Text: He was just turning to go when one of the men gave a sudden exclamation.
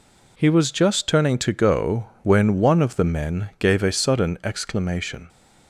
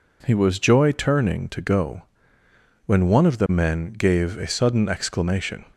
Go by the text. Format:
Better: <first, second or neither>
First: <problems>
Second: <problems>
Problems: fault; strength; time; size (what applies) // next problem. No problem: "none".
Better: first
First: pauses between "go" and "when"; slight; at 2.0 s; 0.16 s long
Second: says "joy" for "just"; at 0.5 s // pauses between "go" and "when"; noticeable; at 2.0 s; 0.82 s long